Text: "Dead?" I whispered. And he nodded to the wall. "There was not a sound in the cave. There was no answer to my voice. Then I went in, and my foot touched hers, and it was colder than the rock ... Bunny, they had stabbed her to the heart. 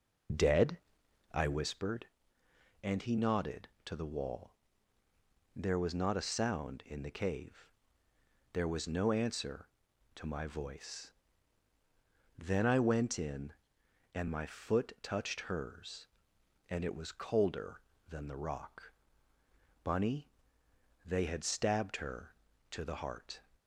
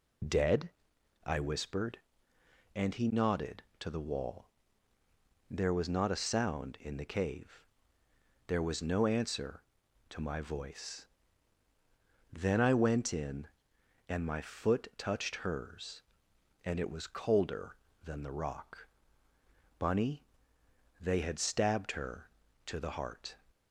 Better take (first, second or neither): second